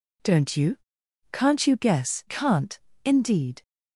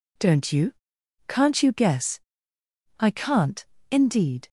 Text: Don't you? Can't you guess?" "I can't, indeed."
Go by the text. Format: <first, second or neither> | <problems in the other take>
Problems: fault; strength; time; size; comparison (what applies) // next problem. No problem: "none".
second | skips "I"; at 2.2 s